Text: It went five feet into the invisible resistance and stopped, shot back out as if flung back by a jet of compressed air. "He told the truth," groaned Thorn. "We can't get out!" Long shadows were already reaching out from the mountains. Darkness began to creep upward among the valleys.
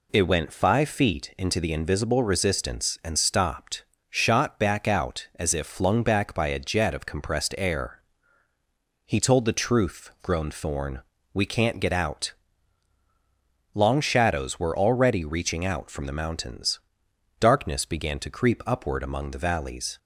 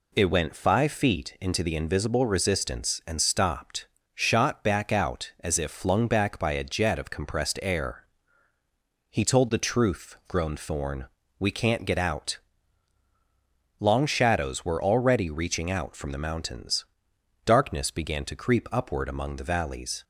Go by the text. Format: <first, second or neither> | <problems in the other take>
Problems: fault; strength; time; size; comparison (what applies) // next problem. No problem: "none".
neither | none